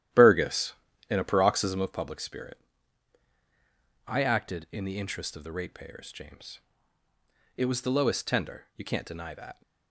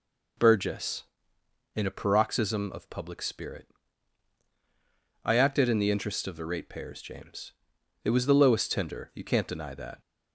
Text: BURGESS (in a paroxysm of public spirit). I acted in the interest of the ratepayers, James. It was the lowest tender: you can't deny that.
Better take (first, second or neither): second